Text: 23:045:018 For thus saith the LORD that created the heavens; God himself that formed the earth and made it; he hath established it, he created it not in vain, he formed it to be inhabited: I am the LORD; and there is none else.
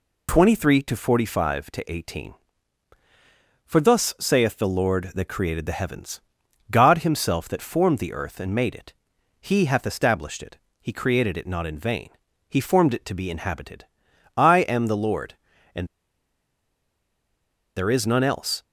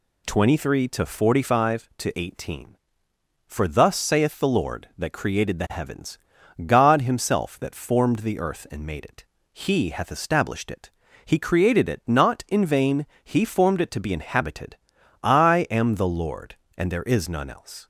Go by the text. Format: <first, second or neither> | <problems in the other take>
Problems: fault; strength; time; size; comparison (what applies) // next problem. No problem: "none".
second | pauses between "and" and "there"; strong; at 15.8 s; 1.8 s long